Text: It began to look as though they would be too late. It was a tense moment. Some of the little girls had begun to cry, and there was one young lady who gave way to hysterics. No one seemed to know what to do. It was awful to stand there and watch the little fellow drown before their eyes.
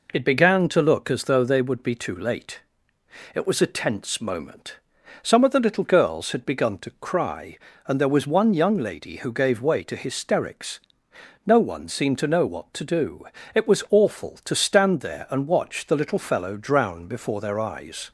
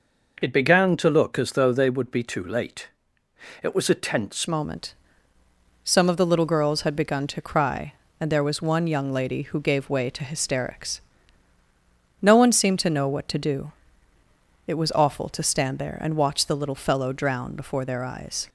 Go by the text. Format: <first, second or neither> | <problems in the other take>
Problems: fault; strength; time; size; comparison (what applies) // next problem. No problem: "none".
first | changes voice at "moment"; from 4.4 s on; 14.0 s long